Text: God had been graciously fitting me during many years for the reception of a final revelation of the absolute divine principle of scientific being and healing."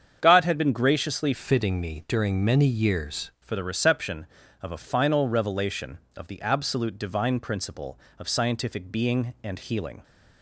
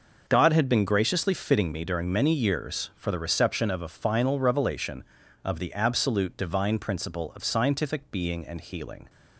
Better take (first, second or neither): second